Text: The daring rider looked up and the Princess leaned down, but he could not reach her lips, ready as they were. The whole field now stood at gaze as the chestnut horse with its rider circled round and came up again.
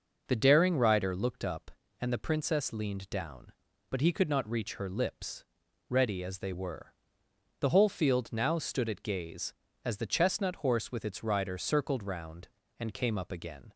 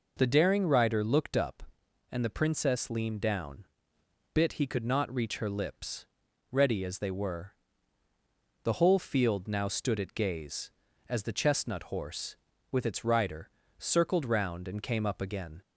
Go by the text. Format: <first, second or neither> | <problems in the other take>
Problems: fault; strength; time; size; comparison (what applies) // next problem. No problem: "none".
first | says "bit" for "but"; at 4.3 s // pauses between "rider" and "circled"; slight; at 13.4 s; 0.27 s long